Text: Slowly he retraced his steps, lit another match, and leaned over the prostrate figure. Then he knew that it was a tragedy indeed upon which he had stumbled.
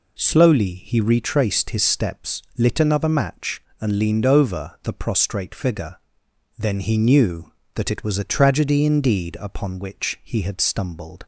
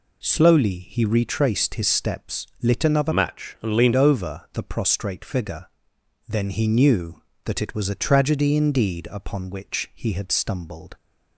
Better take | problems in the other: first | changes voice from "match" to "leaned"; from 3.1 to 3.9 s; 0.8 s long

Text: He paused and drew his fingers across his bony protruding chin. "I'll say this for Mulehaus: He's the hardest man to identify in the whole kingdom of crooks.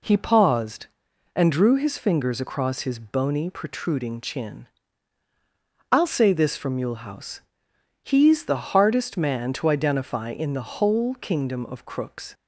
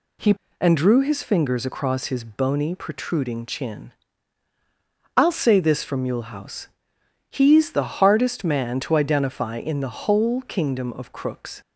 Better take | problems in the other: first | skips "paused"; at 0.4 s

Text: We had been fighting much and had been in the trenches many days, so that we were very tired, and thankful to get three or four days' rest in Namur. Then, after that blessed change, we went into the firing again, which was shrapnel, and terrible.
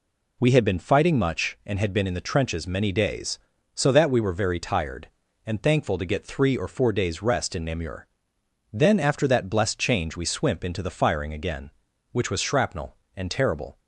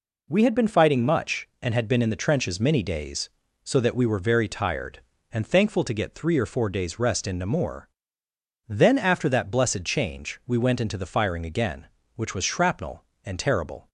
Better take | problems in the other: second | says "swimp" for "went"; at 10.2 s

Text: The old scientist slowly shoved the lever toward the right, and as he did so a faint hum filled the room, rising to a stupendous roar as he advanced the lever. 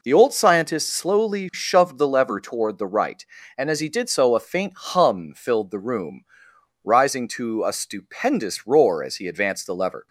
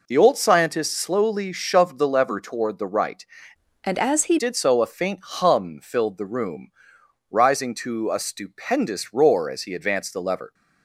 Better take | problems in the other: first | changes voice from "and" to "he"; from 3.8 to 4.3 s; 0.5 s long

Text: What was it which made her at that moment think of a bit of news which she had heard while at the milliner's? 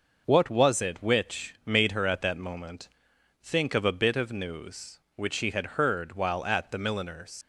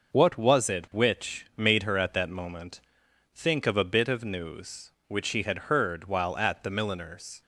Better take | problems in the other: second | pauses between "moment" and "think"; noticeable; at 2.8 s; 0.54 s long; noticeable in the second // leaves "milliner's" unfinished; at 7.4 s; 80 ms

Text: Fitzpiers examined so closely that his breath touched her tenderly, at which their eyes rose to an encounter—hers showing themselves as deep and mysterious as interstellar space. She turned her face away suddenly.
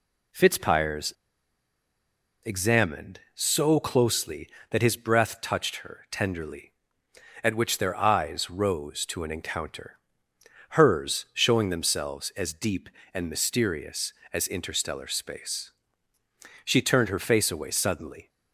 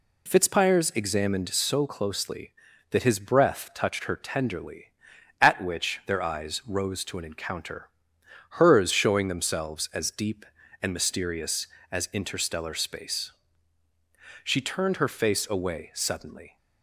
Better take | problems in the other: second | pauses between "Fitzpiers" and "examined"; strong; at 1.1 s; 1.3 s long

